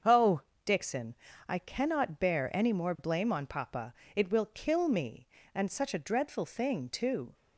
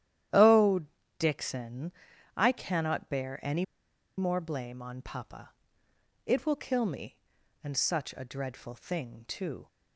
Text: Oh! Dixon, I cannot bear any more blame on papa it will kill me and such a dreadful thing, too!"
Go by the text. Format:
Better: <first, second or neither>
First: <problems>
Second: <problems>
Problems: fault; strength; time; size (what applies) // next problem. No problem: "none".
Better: first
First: starts louder than the rest; until 1.6 s; 7 dB // pauses between "papa" and "it"; slight; at 3.9 s; 0.22 s long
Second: starts louder than the rest; strong; until 1.6 s; 11.5 dB // pauses between "any" and "more"; noticeable; at 3.6 s; 0.53 s long // pauses between "papa" and "it"; noticeable; at 5.5 s; 0.74 s long